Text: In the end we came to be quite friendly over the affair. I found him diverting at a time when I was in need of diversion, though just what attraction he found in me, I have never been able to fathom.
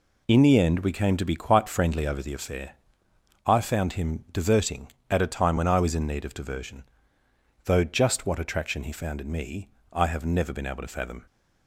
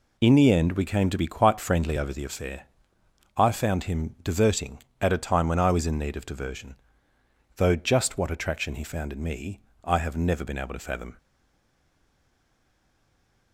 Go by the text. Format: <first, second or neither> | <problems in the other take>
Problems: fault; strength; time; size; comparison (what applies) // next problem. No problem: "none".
first | stays silent after the last word; from 11.1 s on; 2.4 s long